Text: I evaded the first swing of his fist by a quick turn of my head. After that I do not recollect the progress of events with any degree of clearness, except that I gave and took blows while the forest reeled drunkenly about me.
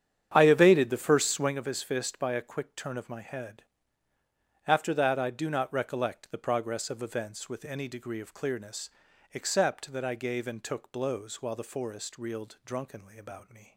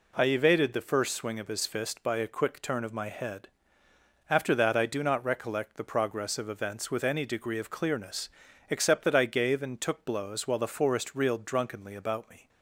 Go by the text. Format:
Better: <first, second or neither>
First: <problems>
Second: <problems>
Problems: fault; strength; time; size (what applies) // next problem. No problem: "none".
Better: second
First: starts louder than the rest; strong; until 1.6 s; 9 dB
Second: none